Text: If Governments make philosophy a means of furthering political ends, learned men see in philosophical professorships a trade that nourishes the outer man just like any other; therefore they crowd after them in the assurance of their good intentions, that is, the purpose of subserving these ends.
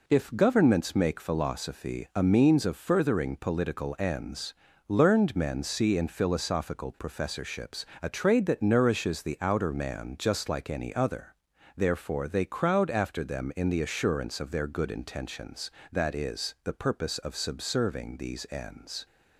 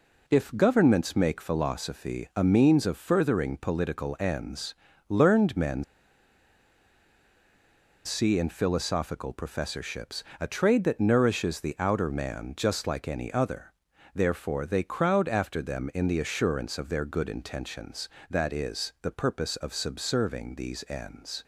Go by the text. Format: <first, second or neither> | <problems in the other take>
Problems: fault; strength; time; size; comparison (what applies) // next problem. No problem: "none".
first | pauses between "men" and "see"; strong; at 5.8 s; 2.2 s long // pauses between "professorships" and "a"; slight; at 10.2 s; 0.16 s long; slight in the first